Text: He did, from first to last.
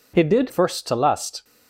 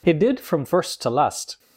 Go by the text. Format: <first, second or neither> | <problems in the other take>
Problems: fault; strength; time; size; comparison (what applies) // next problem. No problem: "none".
second | skips "from"; at 0.4 s